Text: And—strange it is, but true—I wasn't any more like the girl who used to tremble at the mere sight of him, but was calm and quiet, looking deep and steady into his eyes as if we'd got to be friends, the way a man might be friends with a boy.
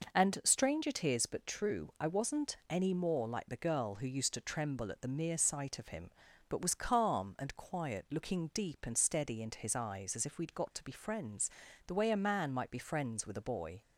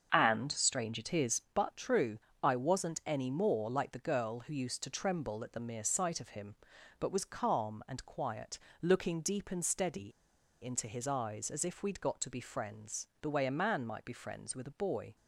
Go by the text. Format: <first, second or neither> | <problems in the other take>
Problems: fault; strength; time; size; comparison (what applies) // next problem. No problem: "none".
first | starts louder than the rest; until 1.1 s; 7 dB // pauses between "steady" and "into"; noticeable; at 10.1 s; 0.49 s long